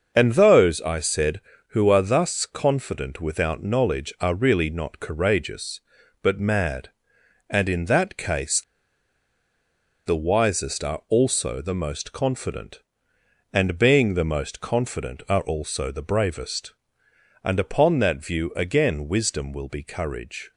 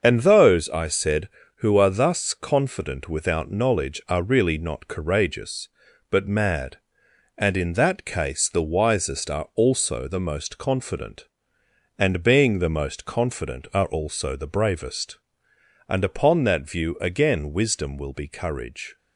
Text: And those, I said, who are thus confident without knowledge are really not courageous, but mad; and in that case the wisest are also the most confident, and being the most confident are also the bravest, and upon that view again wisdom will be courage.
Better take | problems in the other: second | starts louder than the rest; until 1.1 s; 6.5 dB; also in the second // pauses between "case" and "the"; strong; at 8.6 s; 1.4 s long

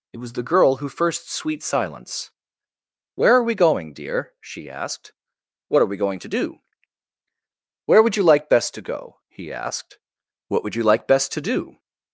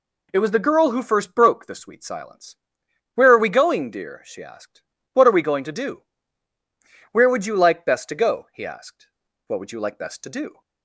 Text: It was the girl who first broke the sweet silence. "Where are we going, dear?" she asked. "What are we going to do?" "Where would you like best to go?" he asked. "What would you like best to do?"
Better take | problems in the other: second | skips "broke the"; at 1.3 s

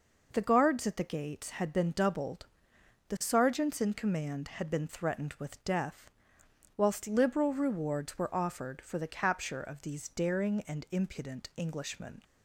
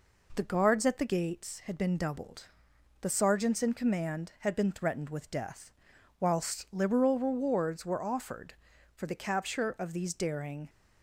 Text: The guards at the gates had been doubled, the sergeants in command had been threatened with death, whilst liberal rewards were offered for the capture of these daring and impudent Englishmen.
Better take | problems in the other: first | stops before "and impudent Englishmen"; at 10.6 s

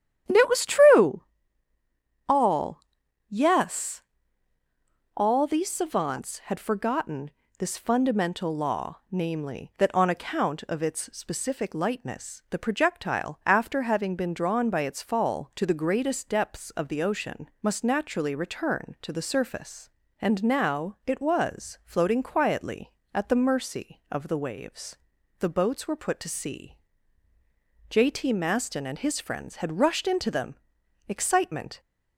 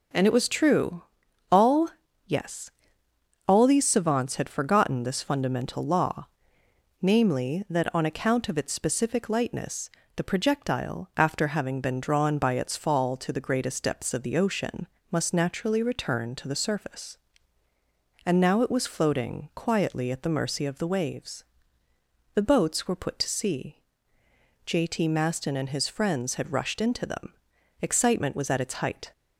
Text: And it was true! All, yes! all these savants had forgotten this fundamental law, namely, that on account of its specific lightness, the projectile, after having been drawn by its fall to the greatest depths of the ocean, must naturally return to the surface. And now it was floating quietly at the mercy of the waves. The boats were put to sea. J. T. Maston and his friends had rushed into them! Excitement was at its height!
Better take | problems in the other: second | starts louder than the rest; strong; until 2.3 s; 10.5 dB // pauses between "forgotten" and "this"; slight; at 7.2 s; 0.28 s long // stops before "was at its height"; at 31.7 s

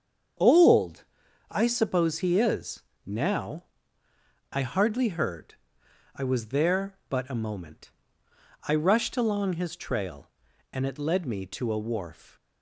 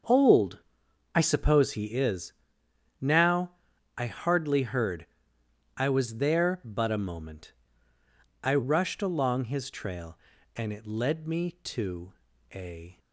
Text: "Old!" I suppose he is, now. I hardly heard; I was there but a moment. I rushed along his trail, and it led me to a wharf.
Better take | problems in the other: first | starts louder than the rest; until 1.6 s; 6.5 dB; strong in the first // pauses between "to" and "a"; at 12.1 s; 0.40 s long // stops before "wharf"; at 12.9 s

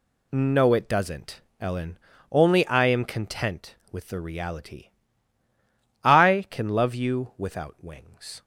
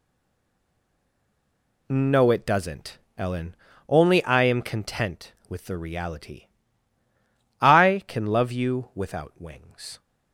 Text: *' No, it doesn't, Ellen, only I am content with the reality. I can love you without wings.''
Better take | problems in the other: first | stays silent before the first word; noticeable; until 1.8 s; 1.8 s long

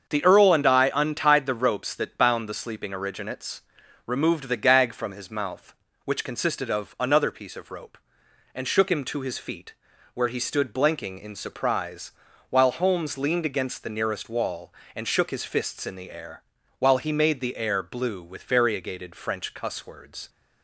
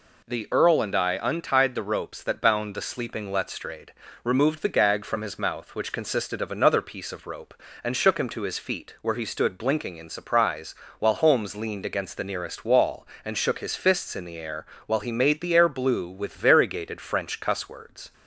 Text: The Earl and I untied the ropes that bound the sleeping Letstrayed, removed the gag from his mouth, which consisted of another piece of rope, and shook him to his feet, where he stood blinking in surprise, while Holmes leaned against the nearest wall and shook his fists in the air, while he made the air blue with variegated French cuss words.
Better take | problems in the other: second | starts louder than the rest; until 1.1 s; 7 dB // says "Originates" for "Letstrayed"; at 2.9 s

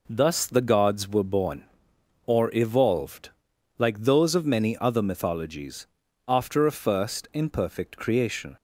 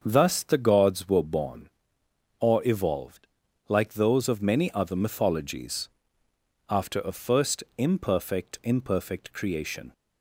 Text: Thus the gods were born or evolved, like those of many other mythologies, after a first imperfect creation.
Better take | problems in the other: first | starts louder than the rest; until 1.0 s; 7 dB // pauses between "first" and "imperfect"; slight; at 7.6 s; 0.16 s long // says "imperfect" twice; at 8.6 s

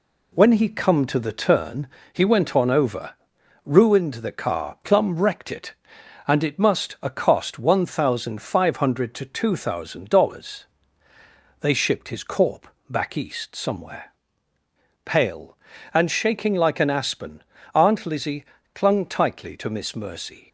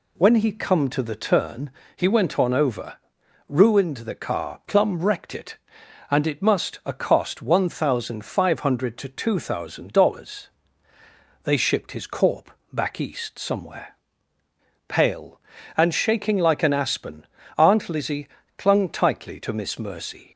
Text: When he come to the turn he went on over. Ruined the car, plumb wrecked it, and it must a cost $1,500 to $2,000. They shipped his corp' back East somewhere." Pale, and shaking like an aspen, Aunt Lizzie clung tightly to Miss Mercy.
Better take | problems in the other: second | gets quieter; noticeable; throughout; 4.5 dB // pauses between "turn" and "he"; slight; at 1.8 s; 0.26 s long; slight in the second // pauses between "corp" and "back"; slight; at 12.6 s; 0.20 s long; slight in the second // pauses between "Lizzie" and "clung"; slight; at 18.4 s; 0.30 s long; slight in the second

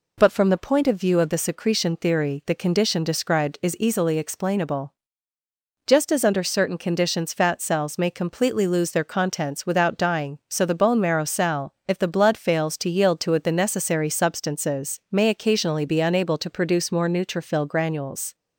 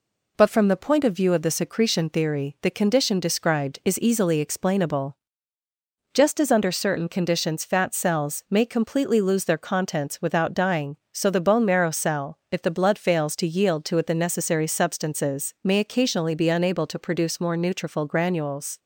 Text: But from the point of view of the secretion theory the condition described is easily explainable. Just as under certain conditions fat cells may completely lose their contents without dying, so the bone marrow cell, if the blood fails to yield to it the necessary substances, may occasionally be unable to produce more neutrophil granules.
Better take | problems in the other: neither | none

